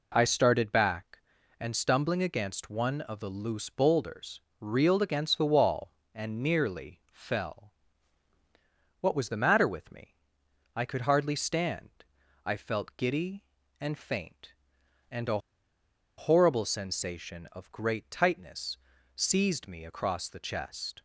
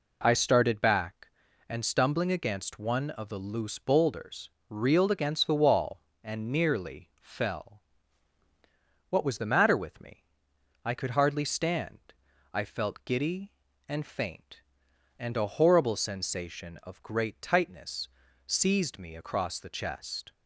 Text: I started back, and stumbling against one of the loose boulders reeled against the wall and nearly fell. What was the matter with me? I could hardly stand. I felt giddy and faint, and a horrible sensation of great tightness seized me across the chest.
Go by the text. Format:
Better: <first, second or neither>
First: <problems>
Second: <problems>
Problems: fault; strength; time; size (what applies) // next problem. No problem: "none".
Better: second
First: pauses between "boulders" and "reeled"; slight; at 4.4 s; 0.20 s long // pauses between "a" and "horrible"; noticeable; at 15.3 s; 0.78 s long // pauses between "tightness" and "seized"; at 18.7 s; 0.38 s long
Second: pauses between "boulders" and "reeled"; slight; at 4.4 s; 0.20 s long // pauses between "tightness" and "seized"; at 18.0 s; 0.38 s long